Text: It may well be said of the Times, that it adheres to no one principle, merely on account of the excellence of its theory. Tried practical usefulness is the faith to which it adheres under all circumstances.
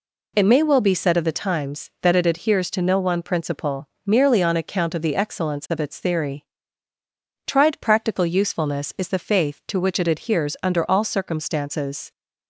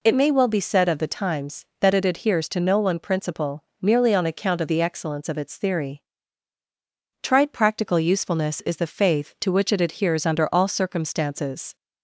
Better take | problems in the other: neither | none

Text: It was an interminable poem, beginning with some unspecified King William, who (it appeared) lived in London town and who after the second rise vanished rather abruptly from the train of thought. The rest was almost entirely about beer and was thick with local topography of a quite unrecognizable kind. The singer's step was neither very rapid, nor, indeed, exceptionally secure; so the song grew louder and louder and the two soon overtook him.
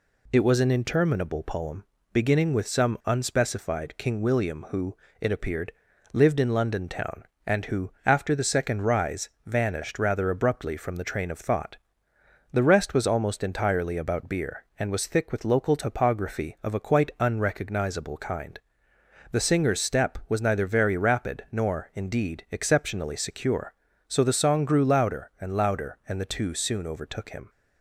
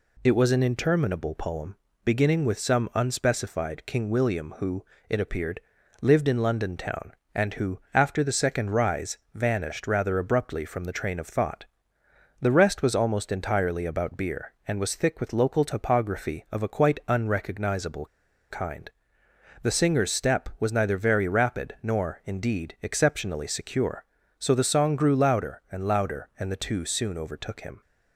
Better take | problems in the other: first | pauses between "who" and "after"; slight; at 7.7 s; 0.16 s long; slight in the first // pauses between "rise" and "vanished"; slight; at 9.1 s; 0.16 s long; slight in the first // pauses between "unrecognizable" and "kind"; at 18.0 s; 0.44 s long

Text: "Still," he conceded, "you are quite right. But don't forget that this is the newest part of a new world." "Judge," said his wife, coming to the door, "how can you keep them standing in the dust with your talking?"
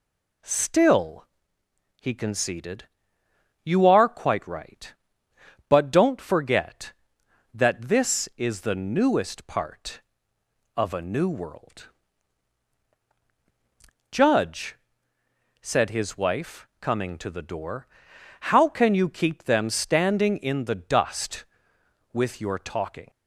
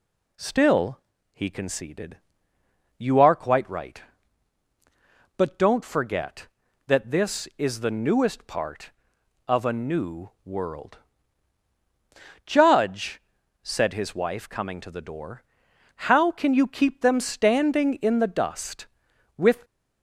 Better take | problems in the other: first | stops before "your talking"; at 19.6 s

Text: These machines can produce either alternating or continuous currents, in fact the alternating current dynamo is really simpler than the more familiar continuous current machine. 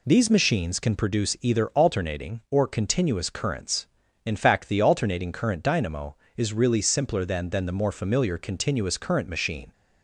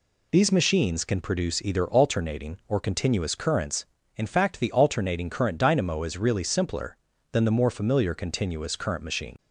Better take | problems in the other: second | says "than" twice; at 7.4 s

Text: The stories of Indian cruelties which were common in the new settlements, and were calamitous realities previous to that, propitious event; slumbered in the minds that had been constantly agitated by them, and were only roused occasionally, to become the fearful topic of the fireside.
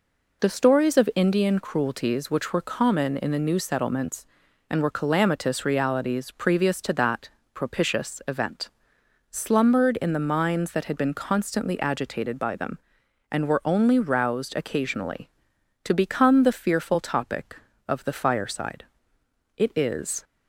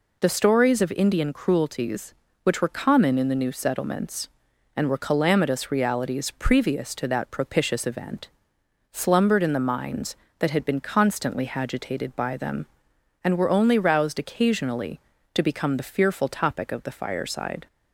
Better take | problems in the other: second | goes on to say "It is"; noticeable; from 19.5 s on; 0.66 s long

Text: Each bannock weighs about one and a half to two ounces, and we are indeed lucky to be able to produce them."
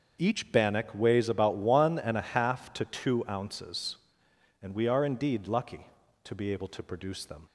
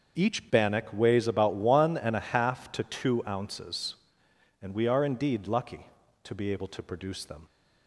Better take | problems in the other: neither | starts louder than the rest; the same in both

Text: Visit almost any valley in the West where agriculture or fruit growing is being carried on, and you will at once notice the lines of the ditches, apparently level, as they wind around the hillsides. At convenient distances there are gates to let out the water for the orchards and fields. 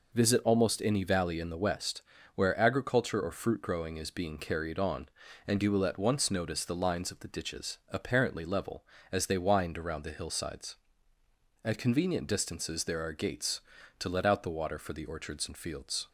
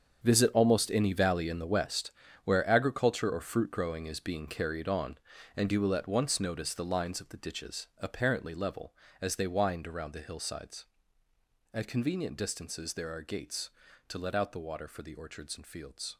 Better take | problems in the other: first | gets quieter; strong; throughout; 13 dB // pauses between "West" and "where"; slight; at 2.1 s; 0.32 s long; slight in the first

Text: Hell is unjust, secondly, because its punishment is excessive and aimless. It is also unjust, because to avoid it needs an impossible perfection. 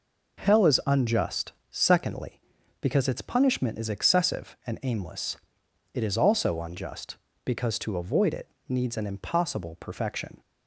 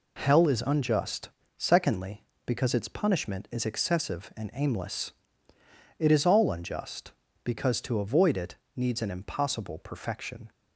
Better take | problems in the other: first | says "all" for "also"; at 6.2 s // pauses between "it" and "needs"; slight; at 8.5 s; 0.22 s long; slight in the first

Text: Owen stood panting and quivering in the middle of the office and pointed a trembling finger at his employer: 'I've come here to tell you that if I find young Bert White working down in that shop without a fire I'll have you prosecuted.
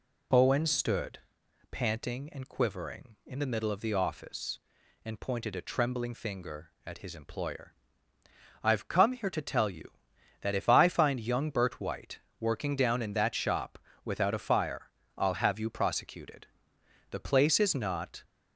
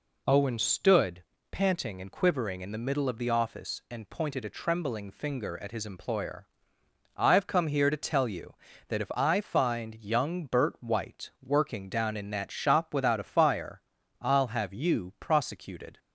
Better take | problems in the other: second | pauses between "stood" and "panting"; noticeable; at 1.1 s; 0.54 s long; slight in the second // pauses between "White" and "working"; slight; at 12.1 s; 0.20 s long // pauses between "shop" and "without"; slight; at 13.7 s; 0.28 s long // pauses between "fire" and "I'll"; slight; at 14.8 s; 0.28 s long; slight in the second // goes on to say "The place is not"; noticeable; from 17.0 s on; 1.1 s long

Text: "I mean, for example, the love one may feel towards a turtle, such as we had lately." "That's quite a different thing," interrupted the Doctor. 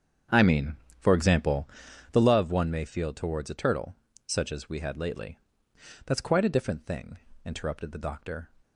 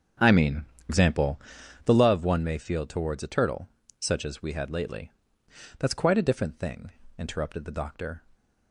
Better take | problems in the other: first | starts louder than the rest; strong; until 1.9 s; 7.5 dB; strong in the first // skips "for"; at 0.7 s

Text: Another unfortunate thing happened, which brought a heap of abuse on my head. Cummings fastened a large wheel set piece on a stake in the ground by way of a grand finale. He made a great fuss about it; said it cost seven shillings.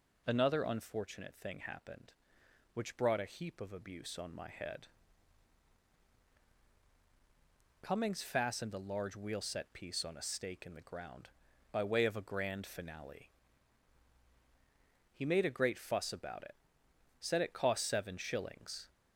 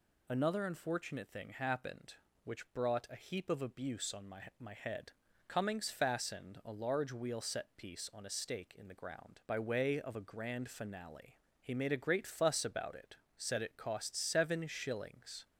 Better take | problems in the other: first | says "my" twice; at 4.5 s

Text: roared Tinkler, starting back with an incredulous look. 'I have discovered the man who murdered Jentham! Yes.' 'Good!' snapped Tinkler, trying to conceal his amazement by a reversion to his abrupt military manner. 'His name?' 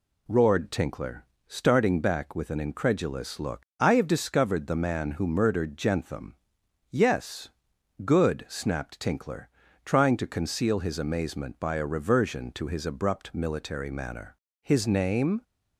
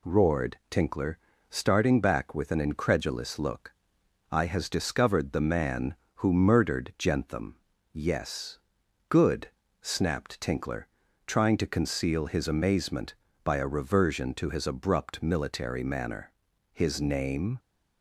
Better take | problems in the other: first | says "has" for "have"; at 4.4 s

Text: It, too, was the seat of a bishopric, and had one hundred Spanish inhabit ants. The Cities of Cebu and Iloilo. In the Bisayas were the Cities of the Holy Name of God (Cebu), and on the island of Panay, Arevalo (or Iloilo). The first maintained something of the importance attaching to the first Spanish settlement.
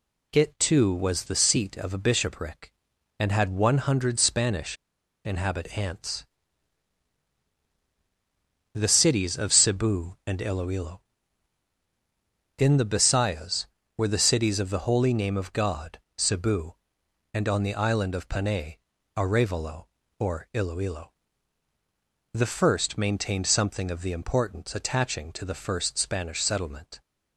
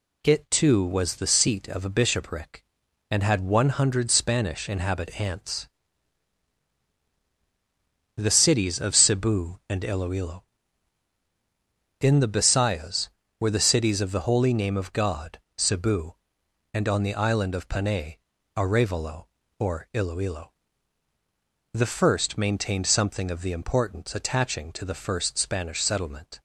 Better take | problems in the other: second | pauses between "Spanish" and "inhabit"; noticeable; at 4.7 s; 0.50 s long

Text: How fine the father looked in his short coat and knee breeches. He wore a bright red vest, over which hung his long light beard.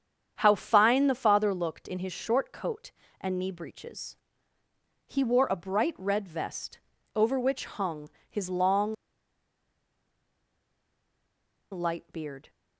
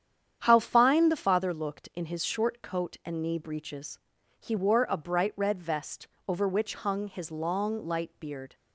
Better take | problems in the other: second | starts louder than the rest; strong; until 1.3 s; 8 dB; strong in the second // pauses between "hung" and "his"; slight; at 8.0 s; 0.22 s long // pauses between "long" and "light"; strong; at 8.9 s; 2.7 s long

